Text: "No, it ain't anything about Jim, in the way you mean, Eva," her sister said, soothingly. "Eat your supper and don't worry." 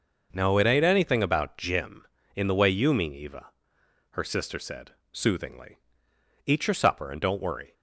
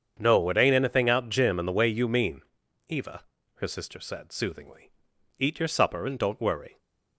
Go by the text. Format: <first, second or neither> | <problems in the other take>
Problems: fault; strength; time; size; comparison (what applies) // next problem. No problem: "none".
first | starts louder than the rest; strong; until 1.2 s; 7.5 dB // says "out" for "about"; at 1.0 s